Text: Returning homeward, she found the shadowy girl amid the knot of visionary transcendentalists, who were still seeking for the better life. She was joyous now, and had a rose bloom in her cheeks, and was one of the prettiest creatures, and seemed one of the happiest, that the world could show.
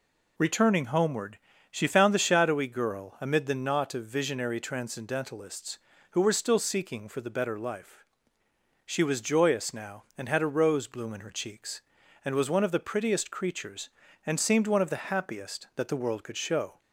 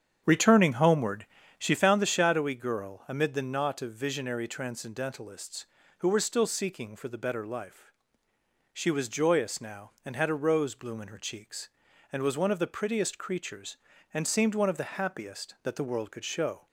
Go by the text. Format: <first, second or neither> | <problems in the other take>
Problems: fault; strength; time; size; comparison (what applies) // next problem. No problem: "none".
first | starts louder than the rest; strong; until 1.8 s; 8.5 dB